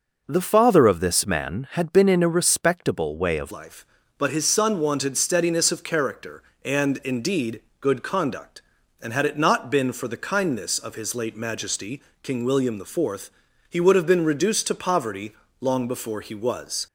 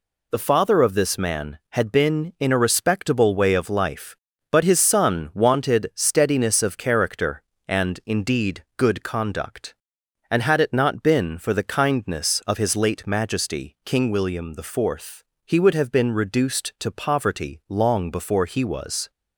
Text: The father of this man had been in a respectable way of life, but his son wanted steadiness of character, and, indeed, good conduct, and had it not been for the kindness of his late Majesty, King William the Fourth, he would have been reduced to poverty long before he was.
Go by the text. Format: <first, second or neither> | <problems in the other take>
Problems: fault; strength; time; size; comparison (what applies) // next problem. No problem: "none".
second | changes voice at "life"; from 3.5 s on; 13.3 s long // pauses between "poverty" and "long"; slight; at 15.3 s; 0.26 s long